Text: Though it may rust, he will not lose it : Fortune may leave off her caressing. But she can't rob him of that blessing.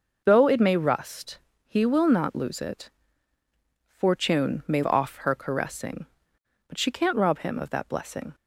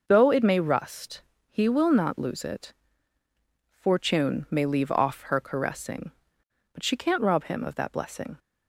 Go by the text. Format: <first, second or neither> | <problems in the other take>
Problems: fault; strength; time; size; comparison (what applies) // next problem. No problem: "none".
second | skips "leave"; at 4.8 s